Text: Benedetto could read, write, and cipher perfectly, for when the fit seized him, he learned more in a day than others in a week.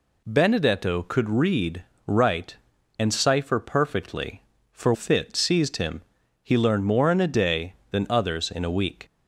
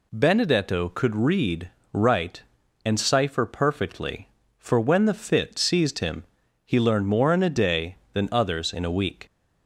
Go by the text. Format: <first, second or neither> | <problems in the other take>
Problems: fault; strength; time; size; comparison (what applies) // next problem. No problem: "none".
second | skips "when the"; at 4.9 s